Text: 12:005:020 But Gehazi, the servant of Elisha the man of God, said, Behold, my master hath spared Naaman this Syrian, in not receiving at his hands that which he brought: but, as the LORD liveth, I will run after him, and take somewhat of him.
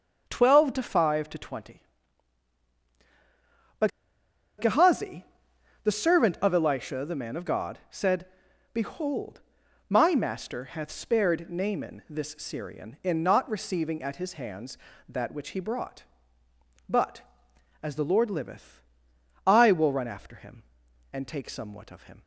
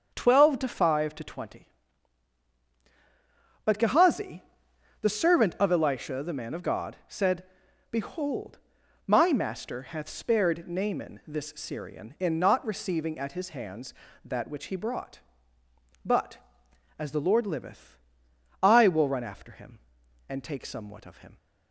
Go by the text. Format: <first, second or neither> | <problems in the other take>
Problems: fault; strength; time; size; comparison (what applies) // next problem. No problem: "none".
second | starts louder than the rest; until 1.3 s; 7 dB; also in the second // pauses between "But" and "Gehazi"; noticeable; at 3.9 s; 0.69 s long